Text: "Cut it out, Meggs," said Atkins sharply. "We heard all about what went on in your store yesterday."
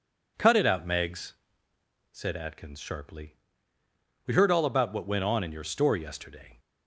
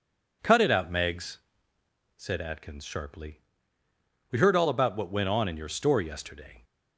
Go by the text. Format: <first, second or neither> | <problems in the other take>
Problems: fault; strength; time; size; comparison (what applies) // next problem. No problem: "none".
neither | none